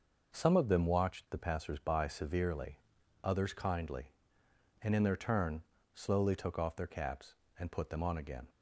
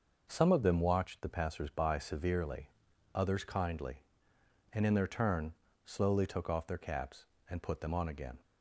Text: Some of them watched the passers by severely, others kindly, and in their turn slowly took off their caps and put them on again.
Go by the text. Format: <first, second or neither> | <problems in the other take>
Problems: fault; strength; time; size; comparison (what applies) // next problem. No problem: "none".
neither | pauses between "turn" and "slowly"; slight; the same in both